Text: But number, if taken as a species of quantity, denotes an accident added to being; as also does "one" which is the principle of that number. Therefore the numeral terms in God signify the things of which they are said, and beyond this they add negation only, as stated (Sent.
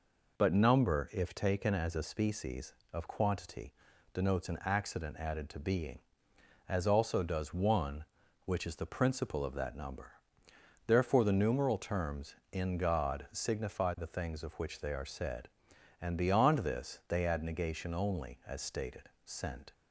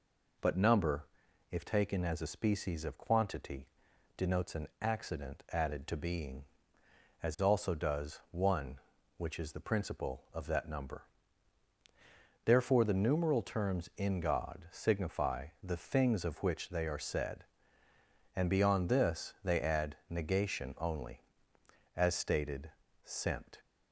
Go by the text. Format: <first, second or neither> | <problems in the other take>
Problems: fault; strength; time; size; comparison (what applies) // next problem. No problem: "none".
neither | none